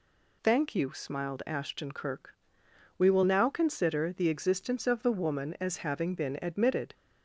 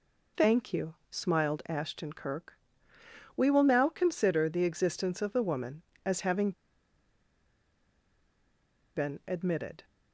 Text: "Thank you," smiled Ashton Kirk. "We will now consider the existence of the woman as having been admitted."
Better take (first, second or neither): first